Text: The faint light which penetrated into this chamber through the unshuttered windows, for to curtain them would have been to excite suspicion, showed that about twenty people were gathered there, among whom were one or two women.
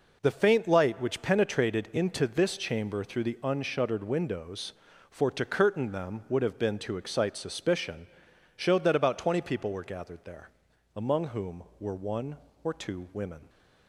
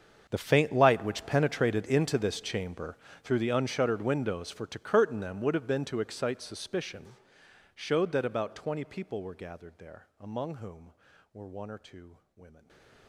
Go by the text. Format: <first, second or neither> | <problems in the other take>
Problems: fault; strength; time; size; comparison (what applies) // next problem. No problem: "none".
first | gets quieter; strong; throughout; 21 dB // pauses between "chamber" and "through"; slight; at 2.9 s; 0.26 s long // pauses between "two" and "women"; slight; at 12.1 s; 0.18 s long // stays silent after the last word; slight; from 12.5 s on; 0.5 s long